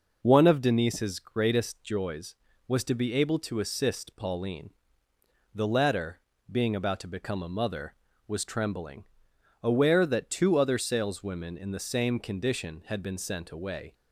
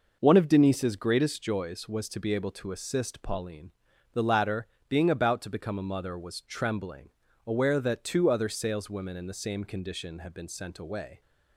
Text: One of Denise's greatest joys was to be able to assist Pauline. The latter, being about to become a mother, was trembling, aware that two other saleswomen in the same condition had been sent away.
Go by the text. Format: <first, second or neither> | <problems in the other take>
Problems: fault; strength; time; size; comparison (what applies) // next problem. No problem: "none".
neither | none